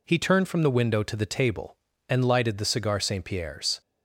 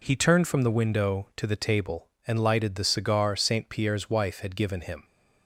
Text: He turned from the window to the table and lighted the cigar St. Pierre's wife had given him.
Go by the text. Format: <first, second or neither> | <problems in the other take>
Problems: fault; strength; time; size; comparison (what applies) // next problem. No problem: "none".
second | stops before "wife had given him"; at 3.8 s